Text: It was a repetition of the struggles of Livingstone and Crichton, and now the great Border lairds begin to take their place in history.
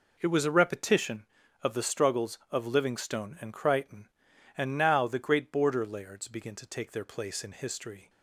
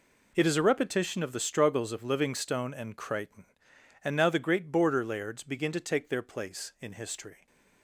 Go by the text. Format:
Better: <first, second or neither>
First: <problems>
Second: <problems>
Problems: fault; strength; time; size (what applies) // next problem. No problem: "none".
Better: first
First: none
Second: says "is" for "was"; at 0.4 s